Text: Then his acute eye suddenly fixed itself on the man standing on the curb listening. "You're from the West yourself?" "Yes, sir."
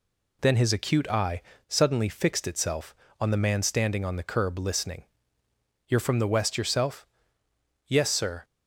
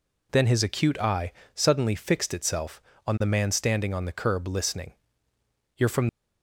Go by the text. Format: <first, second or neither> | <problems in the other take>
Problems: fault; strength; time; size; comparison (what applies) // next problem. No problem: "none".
first | pauses between "eye" and "suddenly"; slight; at 1.3 s; 0.22 s long; slight in the first // stops before "the West yourself Yes sir"; at 6.0 s